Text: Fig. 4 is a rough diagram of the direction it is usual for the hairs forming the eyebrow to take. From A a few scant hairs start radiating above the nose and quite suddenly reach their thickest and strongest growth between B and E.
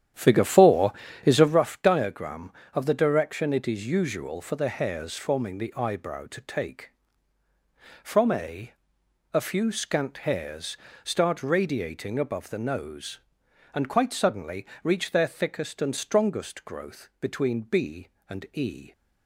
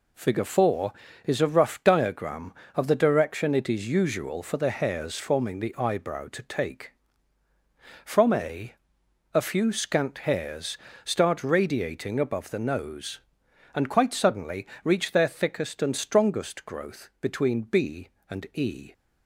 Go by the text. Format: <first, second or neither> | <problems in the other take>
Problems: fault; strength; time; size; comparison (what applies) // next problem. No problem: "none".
second | starts louder than the rest; strong; until 1.6 s; 10 dB // pauses between "A" and "a"; noticeable; at 8.7 s; 0.60 s long; noticeable in the second // pauses between "hairs" and "start"; slight; at 10.7 s; 0.26 s long; slight in the second // pauses between "suddenly" and "reach"; slight; at 14.6 s; 0.16 s long; slight in the second